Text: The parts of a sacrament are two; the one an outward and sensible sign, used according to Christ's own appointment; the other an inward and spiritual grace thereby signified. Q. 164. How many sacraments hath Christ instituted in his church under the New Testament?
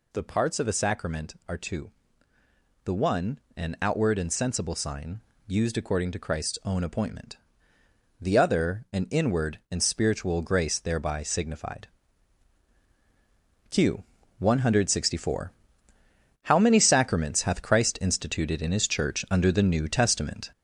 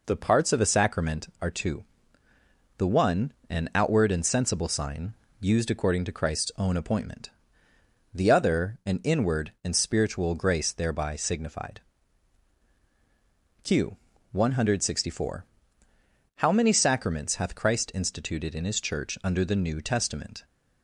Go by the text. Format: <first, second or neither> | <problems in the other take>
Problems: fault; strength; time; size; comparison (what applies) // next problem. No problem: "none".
second | gets louder; noticeable; throughout; 5.5 dB // pauses between "one" and "an"; slight; at 3.3 s; 0.16 s long; slight in the second